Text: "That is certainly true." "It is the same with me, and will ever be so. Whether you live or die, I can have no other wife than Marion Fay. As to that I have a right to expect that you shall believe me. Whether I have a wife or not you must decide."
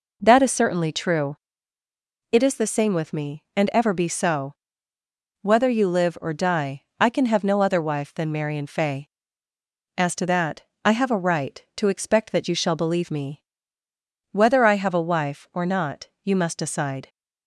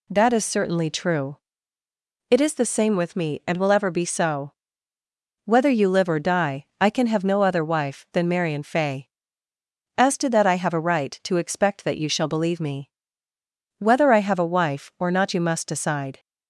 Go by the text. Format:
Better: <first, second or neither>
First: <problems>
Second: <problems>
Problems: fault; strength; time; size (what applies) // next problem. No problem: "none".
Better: second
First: skips "will"; at 3.7 s // pauses between "that" and "I"; slight; at 10.6 s; 0.24 s long // pauses between "not" and "you"; slight; at 16.0 s; 0.16 s long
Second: none